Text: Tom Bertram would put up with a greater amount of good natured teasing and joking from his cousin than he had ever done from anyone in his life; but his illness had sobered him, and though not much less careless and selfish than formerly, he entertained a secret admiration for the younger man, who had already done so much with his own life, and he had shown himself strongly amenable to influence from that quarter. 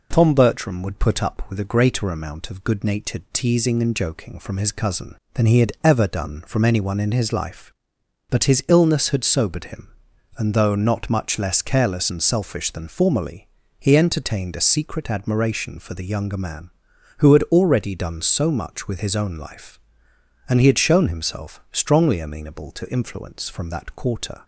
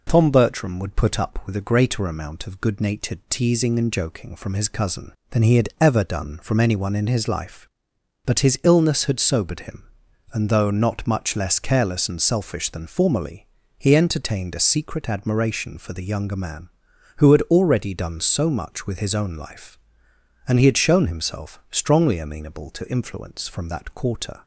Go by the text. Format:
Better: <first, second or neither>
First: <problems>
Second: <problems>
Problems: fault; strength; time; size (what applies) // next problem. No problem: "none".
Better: neither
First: none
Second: none